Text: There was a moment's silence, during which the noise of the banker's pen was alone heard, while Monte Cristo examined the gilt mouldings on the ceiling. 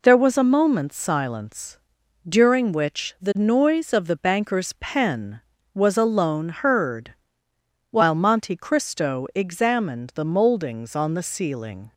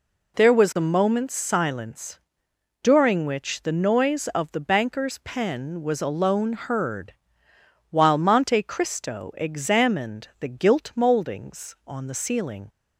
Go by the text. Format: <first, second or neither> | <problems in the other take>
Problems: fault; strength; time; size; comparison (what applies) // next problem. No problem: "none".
second | skips "gilt"; at 10.2 s